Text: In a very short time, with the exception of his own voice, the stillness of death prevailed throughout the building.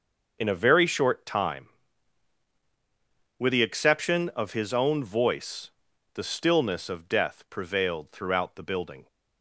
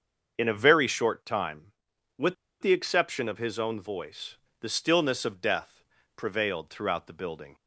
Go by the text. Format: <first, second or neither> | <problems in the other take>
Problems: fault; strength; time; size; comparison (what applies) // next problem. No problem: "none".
first | starts louder than the rest; until 1.3 s; 6.5 dB // pauses between "with" and "the"; slight; at 2.3 s; 0.25 s long // pauses between "death" and "prevailed"; slight; at 5.8 s; 0.34 s long